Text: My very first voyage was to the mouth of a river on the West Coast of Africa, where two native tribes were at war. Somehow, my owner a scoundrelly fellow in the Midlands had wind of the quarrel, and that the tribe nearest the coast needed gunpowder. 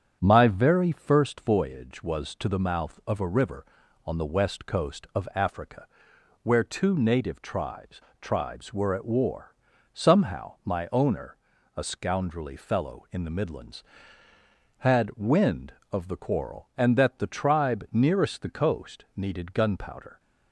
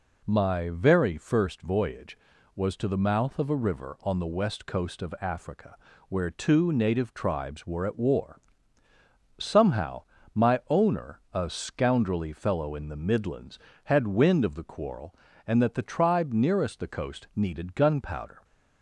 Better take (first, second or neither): second